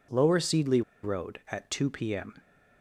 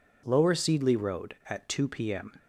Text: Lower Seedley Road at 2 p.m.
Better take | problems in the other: second | pauses between "Seedley" and "Road"; slight; at 0.8 s; 0.21 s long

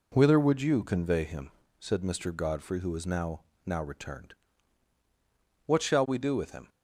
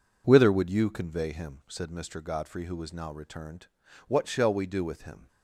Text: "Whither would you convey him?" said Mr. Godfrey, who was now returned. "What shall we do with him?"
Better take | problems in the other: second | says "now" twice; at 3.6 s

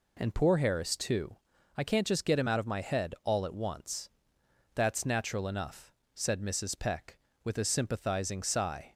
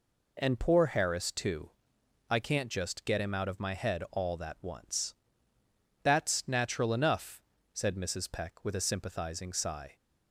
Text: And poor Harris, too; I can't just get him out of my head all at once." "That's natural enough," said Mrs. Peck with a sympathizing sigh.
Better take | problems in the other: first | says "that" for "at"; at 4.3 s

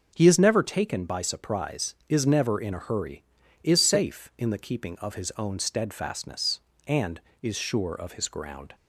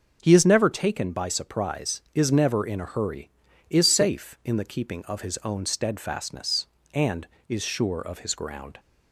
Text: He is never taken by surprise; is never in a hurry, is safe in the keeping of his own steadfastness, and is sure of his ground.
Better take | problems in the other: neither | none

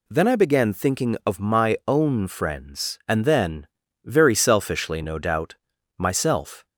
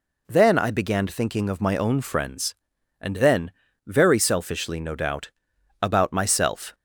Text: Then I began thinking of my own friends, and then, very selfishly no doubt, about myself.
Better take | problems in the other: second | skips "about"; at 5.7 s

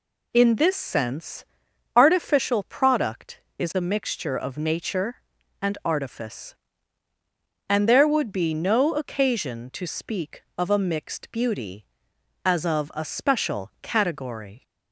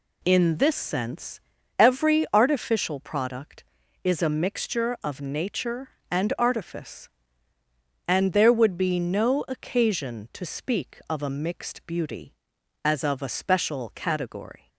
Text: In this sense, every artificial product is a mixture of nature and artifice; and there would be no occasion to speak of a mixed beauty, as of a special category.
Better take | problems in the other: second | skips "every"; at 1.6 s

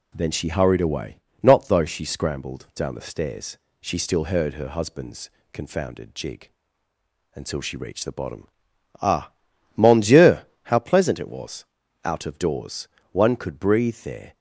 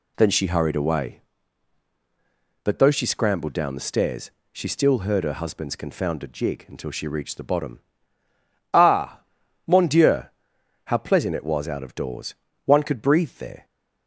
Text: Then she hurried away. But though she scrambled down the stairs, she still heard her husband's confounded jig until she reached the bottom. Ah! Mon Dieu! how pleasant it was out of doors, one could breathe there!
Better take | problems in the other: second | says "Not" for "But"; at 1.4 s // pauses between "husband's" and "confounded"; slight; at 5.2 s; 0.22 s long // pauses between "jig" and "until"; noticeable; at 6.4 s; 0.86 s long // pauses between "was" and "out"; at 11.6 s; 0.40 s long

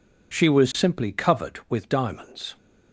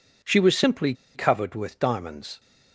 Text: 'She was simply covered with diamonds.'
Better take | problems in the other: first | pauses between "simply" and "covered"; slight; at 0.9 s; 0.21 s long

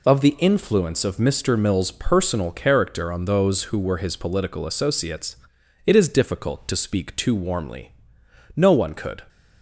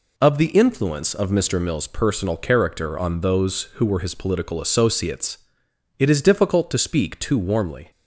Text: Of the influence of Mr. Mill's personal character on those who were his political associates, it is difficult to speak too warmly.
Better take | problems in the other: second | goes on to say "No one could"; noticeable; from 8.5 s on; 0.70 s long

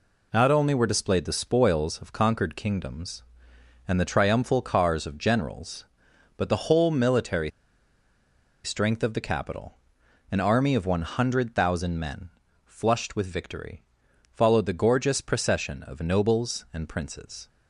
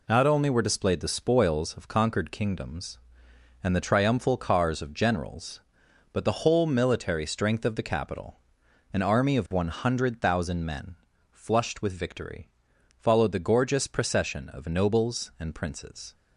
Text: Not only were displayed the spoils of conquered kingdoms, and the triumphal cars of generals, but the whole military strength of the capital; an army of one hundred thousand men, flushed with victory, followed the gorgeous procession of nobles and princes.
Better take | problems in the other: second | pauses between "military" and "strength"; at 7.5 s; 1.1 s long

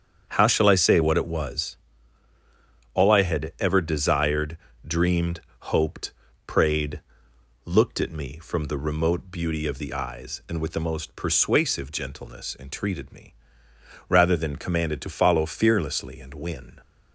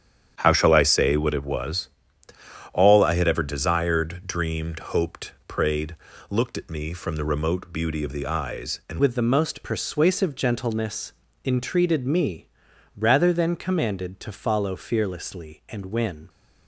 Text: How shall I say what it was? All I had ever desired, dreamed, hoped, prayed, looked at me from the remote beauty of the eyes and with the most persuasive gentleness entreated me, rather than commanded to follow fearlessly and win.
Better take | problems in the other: first | starts louder than the rest; strong; until 1.3 s; 9 dB; strong in the first // changes voice at "with"; from 8.9 s on; 7.3 s long // pauses between "gentleness" and "entreated"; slight; at 11.1 s; 0.32 s long

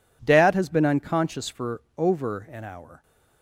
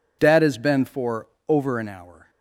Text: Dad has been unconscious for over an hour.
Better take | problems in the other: first | skips "unconscious"; at 0.8 s // pauses between "for" and "over"; slight; at 1.2 s; 0.20 s long; slight in the first

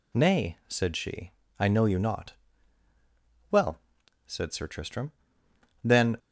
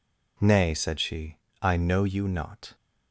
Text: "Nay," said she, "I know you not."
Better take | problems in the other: second | goes on to say "Well said Sir Tristram then"; strong; from 3.5 s on; 2.6 s long

